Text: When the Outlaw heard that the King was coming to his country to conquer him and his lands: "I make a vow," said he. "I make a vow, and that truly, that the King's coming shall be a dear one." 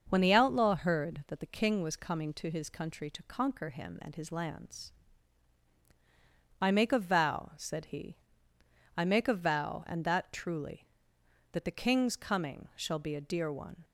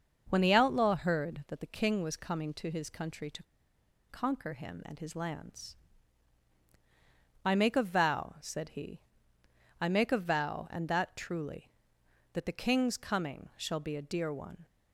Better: first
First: starts louder than the rest; until 1.1 s; 6 dB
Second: starts louder than the rest; until 1.3 s; 6 dB // pauses between "to" and "conquer"; noticeable; at 3.4 s; 0.65 s long

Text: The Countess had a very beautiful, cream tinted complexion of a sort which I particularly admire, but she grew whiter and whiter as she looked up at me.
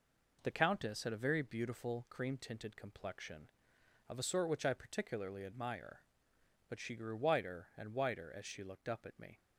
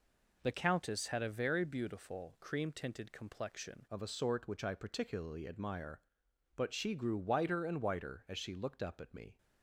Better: first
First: none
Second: changes voice at "of"; from 3.9 s on; 5.4 s long

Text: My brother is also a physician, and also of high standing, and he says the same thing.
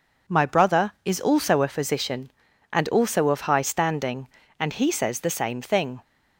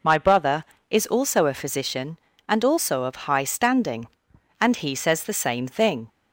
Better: neither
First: none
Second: none

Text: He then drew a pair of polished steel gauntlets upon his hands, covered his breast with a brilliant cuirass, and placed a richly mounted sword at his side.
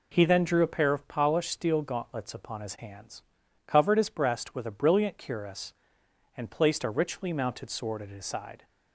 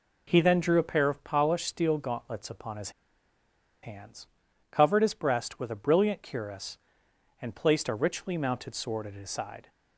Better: first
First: none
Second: pauses between "his" and "hands"; noticeable; at 2.9 s; 0.92 s long

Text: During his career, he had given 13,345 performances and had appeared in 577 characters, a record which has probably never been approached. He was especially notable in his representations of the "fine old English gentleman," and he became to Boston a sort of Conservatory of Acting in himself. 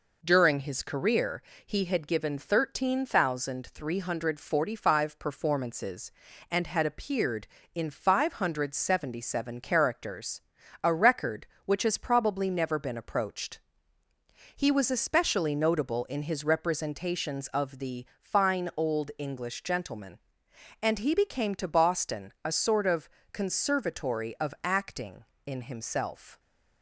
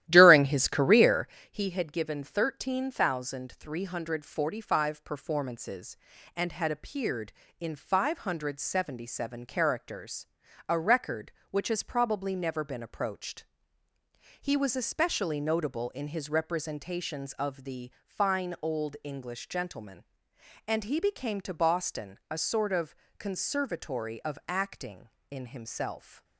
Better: first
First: pauses between "of" and "Conservatory"; slight; at 23.0 s; 0.24 s long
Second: starts louder than the rest; strong; until 1.5 s; 13 dB // pauses between "of" and "Conservatory"; slight; at 22.9 s; 0.24 s long

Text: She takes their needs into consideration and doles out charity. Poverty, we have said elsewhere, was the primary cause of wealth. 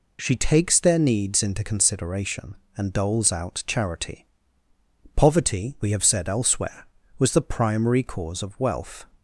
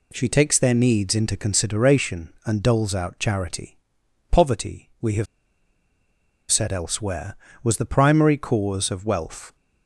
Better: first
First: none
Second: pauses between "have" and "said"; strong; at 5.2 s; 1.2 s long

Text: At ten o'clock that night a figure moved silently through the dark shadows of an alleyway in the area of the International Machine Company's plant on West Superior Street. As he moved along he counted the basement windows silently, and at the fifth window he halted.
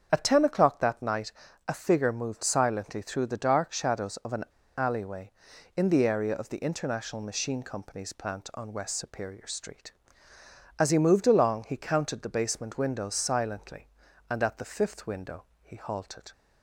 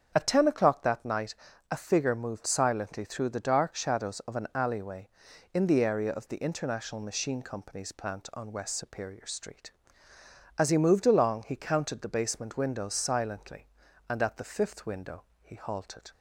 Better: second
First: starts louder than the rest; strong; until 1.1 s; 7.5 dB // pauses between "night" and "a"; slight; at 1.3 s; 0.36 s long // pauses between "an" and "alleyway"; slight; at 4.4 s; 0.32 s long // pauses between "window" and "he"; slight; at 15.4 s; 0.20 s long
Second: starts louder than the rest; strong; until 1.1 s; 7.5 dB // pauses between "night" and "a"; slight; at 1.3 s; 0.36 s long // pauses between "window" and "he"; slight; at 15.2 s; 0.20 s long

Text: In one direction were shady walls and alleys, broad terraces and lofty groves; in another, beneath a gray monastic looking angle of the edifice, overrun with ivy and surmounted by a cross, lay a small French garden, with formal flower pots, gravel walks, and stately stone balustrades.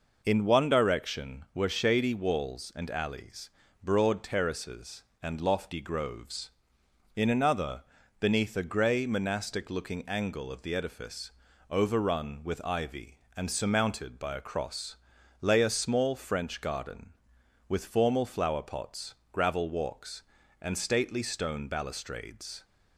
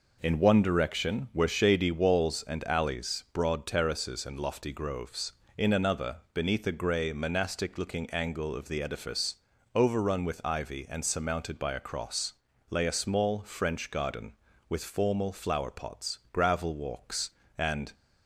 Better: first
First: none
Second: stops before "stately stone balustrades"; at 17.9 s

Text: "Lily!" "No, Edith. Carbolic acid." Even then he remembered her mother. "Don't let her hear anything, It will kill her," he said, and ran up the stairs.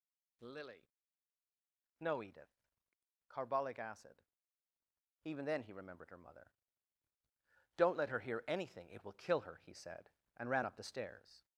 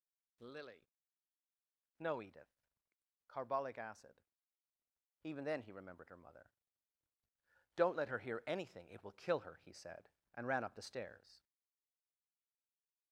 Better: first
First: none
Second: stays silent after the last word; noticeable; from 11.4 s on; 1.7 s long

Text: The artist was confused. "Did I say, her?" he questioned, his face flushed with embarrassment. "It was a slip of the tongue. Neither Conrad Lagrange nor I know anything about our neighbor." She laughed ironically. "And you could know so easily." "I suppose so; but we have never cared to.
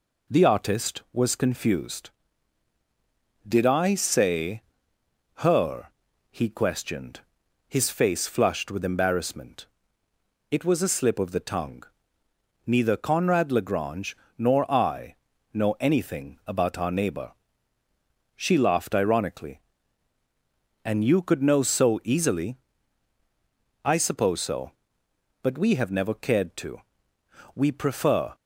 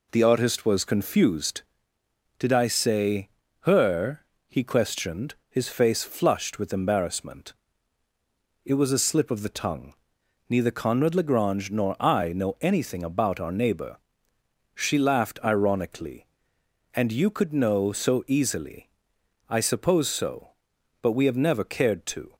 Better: second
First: pauses between "Lagrange" and "nor"; slight; at 14.1 s; 0.22 s long // pauses between "I" and "know"; slight; at 15.1 s; 0.36 s long // goes on to say "We prefer"; noticeable; from 27.5 s on; 0.80 s long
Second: none

